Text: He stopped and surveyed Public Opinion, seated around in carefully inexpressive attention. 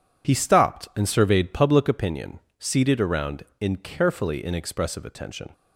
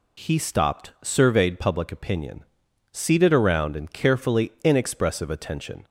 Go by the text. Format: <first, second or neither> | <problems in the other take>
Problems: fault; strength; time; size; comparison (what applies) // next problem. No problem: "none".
first | skips "and"; at 0.9 s